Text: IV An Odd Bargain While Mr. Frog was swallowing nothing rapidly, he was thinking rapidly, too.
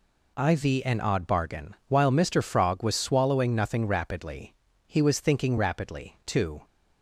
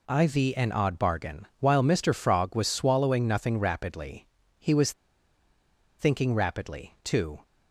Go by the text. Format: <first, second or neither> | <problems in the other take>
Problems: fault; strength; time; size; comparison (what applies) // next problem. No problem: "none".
first | pauses between "was" and "thinking"; at 4.9 s; 1.0 s long